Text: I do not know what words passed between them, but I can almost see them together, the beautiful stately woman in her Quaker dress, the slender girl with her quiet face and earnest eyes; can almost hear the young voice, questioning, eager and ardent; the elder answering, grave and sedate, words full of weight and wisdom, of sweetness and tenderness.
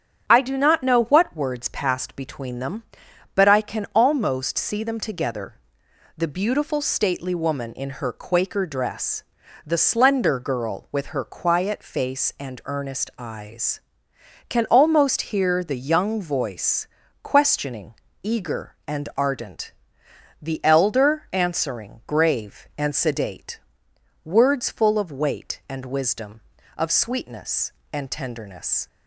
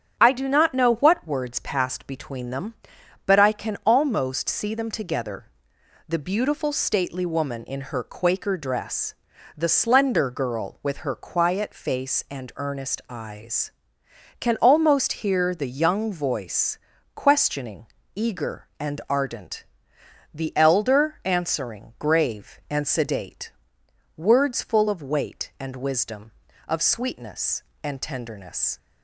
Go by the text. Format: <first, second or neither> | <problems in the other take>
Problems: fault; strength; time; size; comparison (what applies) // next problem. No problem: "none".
neither | starts louder than the rest; strong; the same in both